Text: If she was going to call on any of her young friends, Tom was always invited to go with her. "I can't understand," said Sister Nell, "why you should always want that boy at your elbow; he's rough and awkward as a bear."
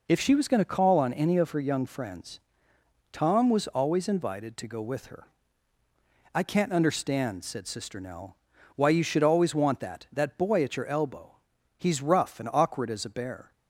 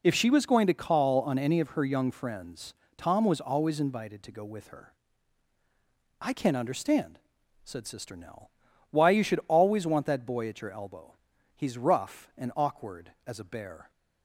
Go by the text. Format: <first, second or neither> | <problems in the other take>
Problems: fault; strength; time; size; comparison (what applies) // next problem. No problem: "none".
second | says "that" twice; at 10.1 s